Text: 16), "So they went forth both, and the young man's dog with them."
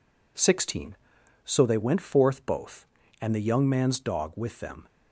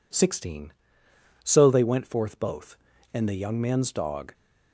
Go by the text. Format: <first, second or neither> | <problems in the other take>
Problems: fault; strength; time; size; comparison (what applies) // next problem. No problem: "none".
first | stops before "with them"; at 4.3 s